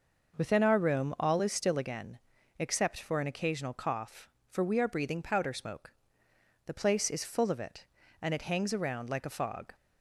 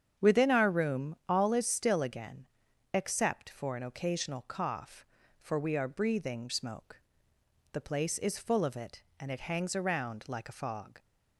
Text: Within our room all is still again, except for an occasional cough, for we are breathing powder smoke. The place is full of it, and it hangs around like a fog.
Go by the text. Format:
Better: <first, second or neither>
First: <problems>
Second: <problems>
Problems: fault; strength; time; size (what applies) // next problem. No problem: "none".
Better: first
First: none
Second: starts louder than the rest; strong; until 1.3 s; 8 dB // skips "powder"; at 6.4 s